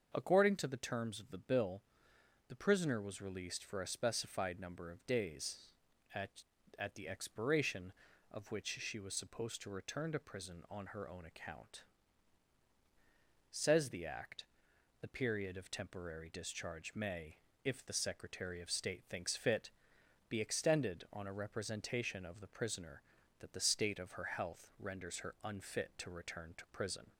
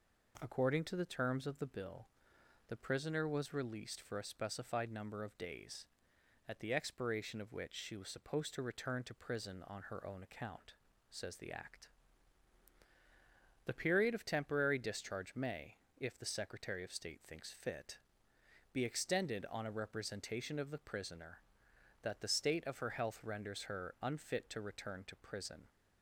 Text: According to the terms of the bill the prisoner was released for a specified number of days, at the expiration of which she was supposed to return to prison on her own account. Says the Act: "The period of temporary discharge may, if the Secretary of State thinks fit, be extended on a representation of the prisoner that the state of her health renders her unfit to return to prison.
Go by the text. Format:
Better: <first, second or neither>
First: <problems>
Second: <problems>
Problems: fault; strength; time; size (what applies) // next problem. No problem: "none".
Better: second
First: starts louder than the rest; until 1.1 s; 6.5 dB // pauses between "bill" and "the"; noticeable; at 1.8 s; 0.66 s long // says "at" twice; at 6.7 s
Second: pauses between "bill" and "the"; noticeable; at 2.0 s; 0.60 s long